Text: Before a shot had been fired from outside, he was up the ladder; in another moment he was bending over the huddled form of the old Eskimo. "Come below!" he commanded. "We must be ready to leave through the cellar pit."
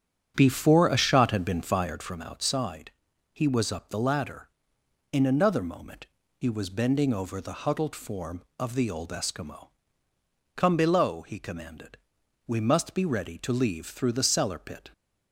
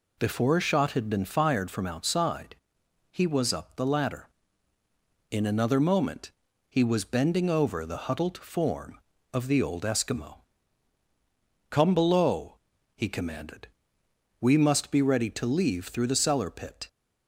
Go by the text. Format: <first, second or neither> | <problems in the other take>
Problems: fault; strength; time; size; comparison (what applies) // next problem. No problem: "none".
second | starts louder than the rest; strong; until 2.1 s; 8.5 dB // pauses between "moment" and "he"; slight; at 6.0 s; 0.30 s long; slight in the second